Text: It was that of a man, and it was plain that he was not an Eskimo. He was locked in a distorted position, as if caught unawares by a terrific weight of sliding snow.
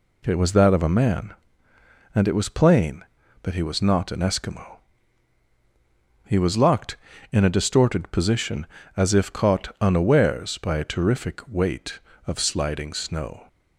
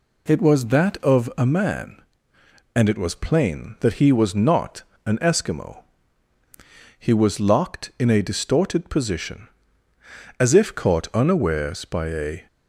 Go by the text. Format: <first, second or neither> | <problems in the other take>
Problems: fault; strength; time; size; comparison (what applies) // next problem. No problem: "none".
first | pauses between "not" and "an"; slight; at 4.8 s; 0.22 s long // stops before "terrific weight of sliding snow"; at 12.4 s